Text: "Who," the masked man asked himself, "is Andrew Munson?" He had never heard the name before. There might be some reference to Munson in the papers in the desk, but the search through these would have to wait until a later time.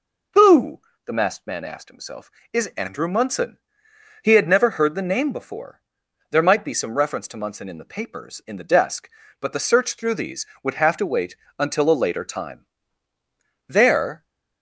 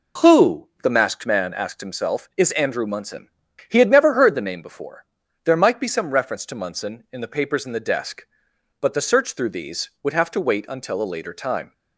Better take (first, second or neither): second